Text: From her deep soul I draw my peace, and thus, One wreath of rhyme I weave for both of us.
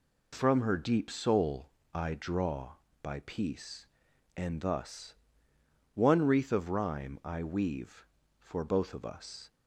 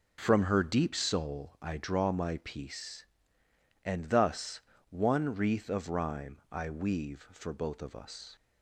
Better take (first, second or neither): second